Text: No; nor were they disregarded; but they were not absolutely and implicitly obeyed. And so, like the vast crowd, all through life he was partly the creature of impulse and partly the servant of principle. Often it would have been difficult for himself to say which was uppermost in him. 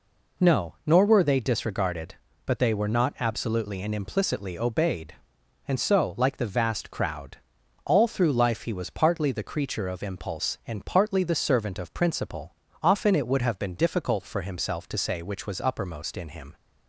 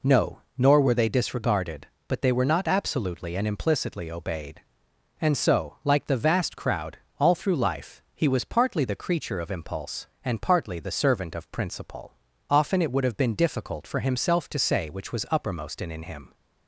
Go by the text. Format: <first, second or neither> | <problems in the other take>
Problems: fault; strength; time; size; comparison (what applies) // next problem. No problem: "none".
first | says "in" twice; at 15.9 s